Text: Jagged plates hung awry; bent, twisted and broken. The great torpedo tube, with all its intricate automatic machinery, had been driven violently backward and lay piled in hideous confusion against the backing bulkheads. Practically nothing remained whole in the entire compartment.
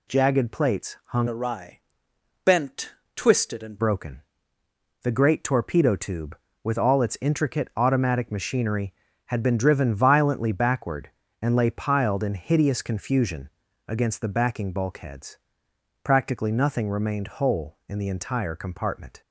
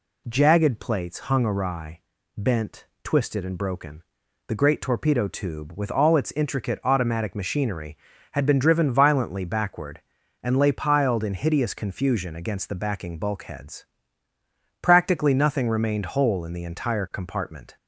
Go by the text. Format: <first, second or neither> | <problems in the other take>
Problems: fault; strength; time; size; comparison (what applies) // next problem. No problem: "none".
second | changes voice from "awry" to "and"; from 1.2 to 3.7 s; 2.5 s long // pauses between "confusion" and "against"; slight; at 13.5 s; 0.36 s long